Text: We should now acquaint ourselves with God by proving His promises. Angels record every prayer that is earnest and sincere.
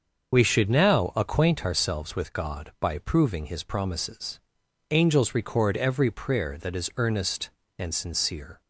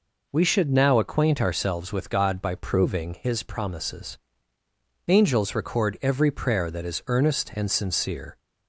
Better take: second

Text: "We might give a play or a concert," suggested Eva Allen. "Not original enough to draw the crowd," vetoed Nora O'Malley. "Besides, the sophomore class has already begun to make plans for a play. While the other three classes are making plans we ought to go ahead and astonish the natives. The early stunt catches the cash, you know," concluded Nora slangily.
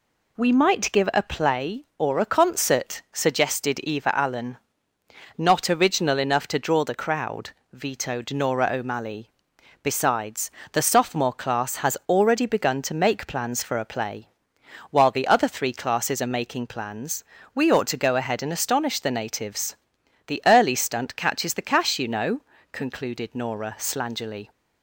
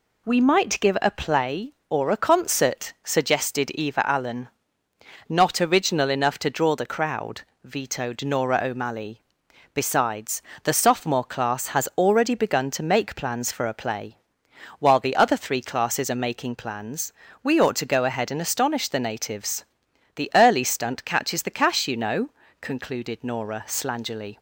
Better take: neither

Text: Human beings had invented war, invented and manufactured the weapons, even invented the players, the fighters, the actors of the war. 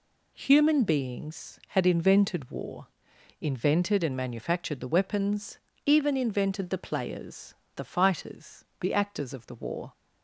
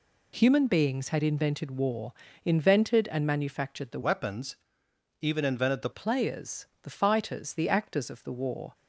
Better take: first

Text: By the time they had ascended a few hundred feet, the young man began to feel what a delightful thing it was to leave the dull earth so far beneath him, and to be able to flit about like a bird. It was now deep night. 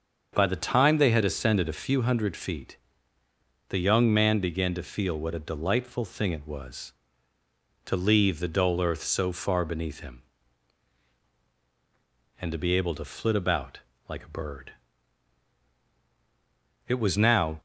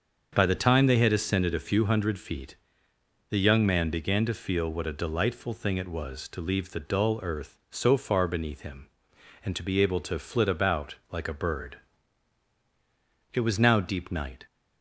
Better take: second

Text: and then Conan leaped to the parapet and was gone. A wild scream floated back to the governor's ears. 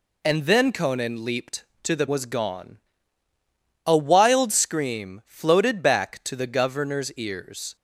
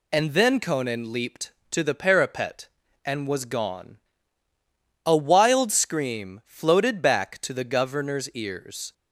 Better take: second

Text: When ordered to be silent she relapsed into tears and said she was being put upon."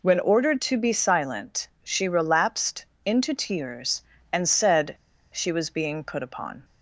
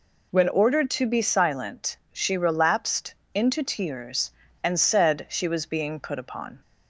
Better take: second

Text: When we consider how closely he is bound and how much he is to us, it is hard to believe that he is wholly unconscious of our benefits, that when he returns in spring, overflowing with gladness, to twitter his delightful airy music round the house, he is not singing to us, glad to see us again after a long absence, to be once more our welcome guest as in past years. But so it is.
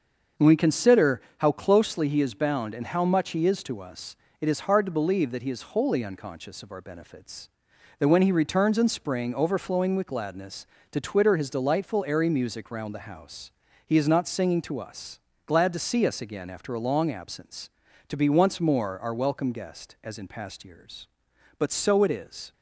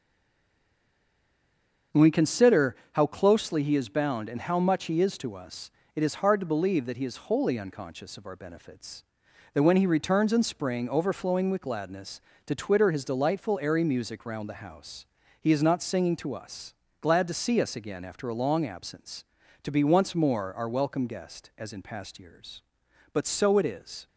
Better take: first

